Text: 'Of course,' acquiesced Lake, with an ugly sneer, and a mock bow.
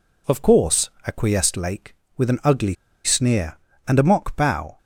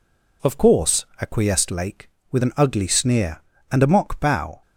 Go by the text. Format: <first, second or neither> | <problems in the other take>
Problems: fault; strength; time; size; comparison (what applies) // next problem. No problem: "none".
second | pauses between "ugly" and "sneer"; slight; at 2.7 s; 0.30 s long